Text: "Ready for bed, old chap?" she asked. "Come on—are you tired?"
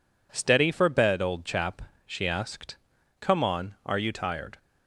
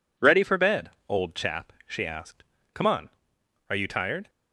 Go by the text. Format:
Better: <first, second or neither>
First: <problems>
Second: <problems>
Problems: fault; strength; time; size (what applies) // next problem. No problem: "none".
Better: second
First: says "Steady" for "Ready"; at 0.3 s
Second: none